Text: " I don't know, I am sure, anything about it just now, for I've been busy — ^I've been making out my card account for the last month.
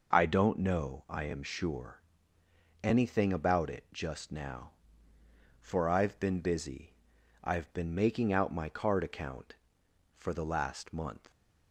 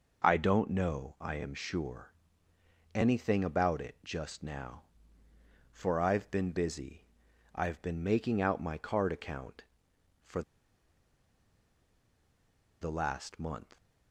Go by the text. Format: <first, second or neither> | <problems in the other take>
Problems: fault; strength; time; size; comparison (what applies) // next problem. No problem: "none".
first | pauses between "for" and "the"; strong; at 10.4 s; 2.4 s long